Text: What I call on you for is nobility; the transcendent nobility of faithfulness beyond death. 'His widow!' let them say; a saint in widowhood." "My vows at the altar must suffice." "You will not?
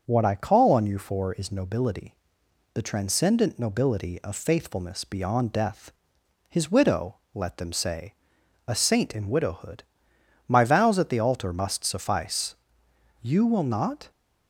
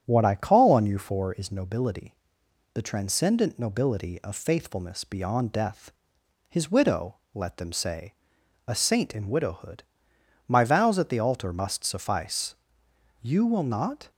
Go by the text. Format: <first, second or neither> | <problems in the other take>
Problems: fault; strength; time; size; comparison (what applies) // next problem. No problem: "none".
first | starts louder than the rest; strong; until 1.4 s; 9 dB